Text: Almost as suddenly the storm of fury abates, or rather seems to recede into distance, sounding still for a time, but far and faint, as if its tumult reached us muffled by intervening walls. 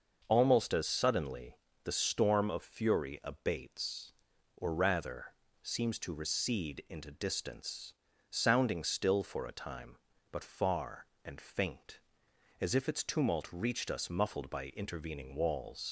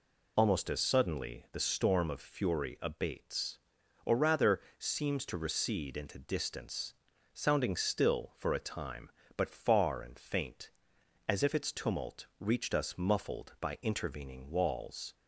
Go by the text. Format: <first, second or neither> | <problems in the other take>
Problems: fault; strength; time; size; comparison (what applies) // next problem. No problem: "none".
second | starts louder than the rest; noticeable; until 1.2 s; 6 dB // pauses between "suddenly" and "the"; slight; at 1.5 s; 0.26 s long // pauses between "rather" and "seems"; slight; at 5.3 s; 0.28 s long; slight in the second // leaves "walls" unfinished; at 15.8 s; 95 ms